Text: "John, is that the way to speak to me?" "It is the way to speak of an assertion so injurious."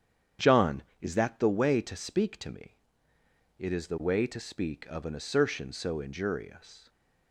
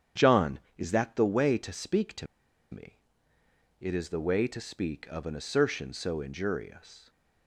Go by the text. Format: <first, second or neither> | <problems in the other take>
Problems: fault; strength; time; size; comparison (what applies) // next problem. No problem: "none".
first | starts louder than the rest; strong; until 1.3 s; 9 dB; strong in the first // pauses between "to" and "me"; at 2.2 s; 0.45 s long